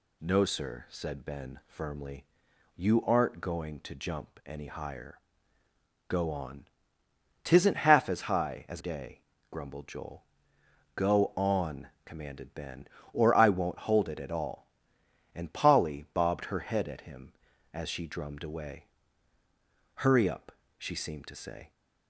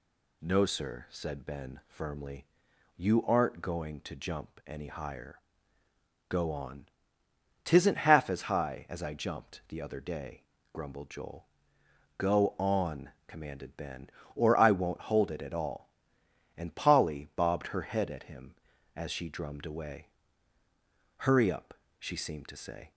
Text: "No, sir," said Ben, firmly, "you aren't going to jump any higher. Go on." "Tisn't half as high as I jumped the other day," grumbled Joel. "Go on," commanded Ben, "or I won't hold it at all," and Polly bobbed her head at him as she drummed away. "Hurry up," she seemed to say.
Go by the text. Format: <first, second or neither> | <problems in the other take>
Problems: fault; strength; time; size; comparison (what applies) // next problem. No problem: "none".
second | skips "I jumped the other"; at 8.8 s